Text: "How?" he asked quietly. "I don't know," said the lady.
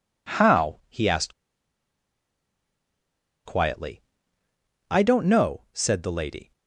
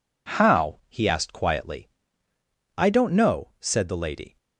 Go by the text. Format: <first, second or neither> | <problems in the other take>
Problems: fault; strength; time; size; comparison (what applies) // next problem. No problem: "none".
second | pauses between "asked" and "quietly"; strong; at 1.3 s; 2.1 s long